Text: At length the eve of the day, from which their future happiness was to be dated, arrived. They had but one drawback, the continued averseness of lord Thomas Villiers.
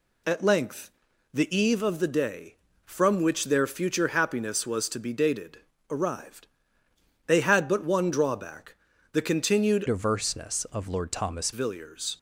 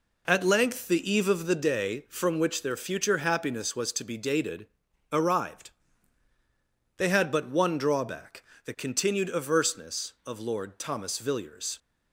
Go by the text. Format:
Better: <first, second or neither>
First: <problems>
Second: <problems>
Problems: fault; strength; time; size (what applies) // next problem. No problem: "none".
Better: second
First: pauses between "length" and "the"; at 0.8 s; 0.44 s long // changes voice from "averseness" to "Thomas"; from 9.8 to 11.5 s; 1.7 s long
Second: none